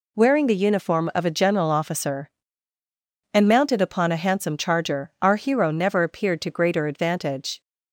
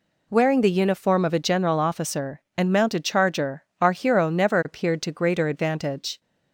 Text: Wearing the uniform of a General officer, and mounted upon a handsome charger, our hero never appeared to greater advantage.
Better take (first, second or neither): first